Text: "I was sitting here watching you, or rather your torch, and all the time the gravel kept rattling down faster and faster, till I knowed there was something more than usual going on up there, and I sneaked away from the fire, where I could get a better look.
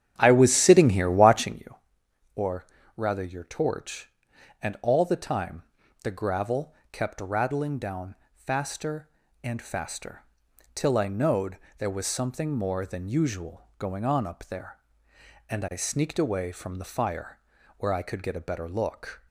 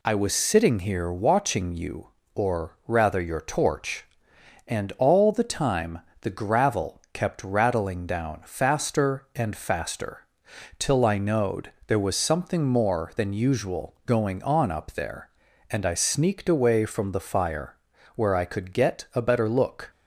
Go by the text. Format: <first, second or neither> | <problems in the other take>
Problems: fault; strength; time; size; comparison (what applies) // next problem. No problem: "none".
second | starts louder than the rest; strong; until 1.7 s; 9.5 dB // pauses between "or" and "rather"; slight; at 2.6 s; 0.30 s long // pauses between "time" and "the"; at 5.6 s; 0.40 s long; slight in the second // pauses between "gravel" and "kept"; slight; at 6.7 s; 0.18 s long // pauses between "down" and "faster"; slight; at 8.1 s; 0.16 s long // pauses between "knowed" and "there"; slight; at 11.5 s; 0.20 s long